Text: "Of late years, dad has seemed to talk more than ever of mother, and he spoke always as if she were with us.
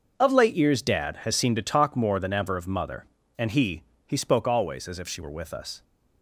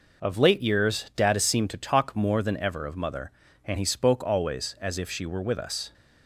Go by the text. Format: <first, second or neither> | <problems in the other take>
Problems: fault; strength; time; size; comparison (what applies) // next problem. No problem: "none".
second | starts louder than the rest; noticeable; until 1.1 s; 6 dB // says "he" twice; at 4.0 s